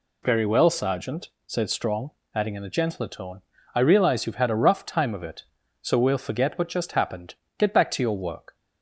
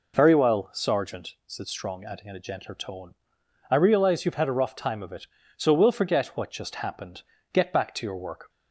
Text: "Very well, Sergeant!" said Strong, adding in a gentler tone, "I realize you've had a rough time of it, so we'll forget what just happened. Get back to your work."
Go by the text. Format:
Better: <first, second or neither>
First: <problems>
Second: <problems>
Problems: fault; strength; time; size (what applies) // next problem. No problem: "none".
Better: neither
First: none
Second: none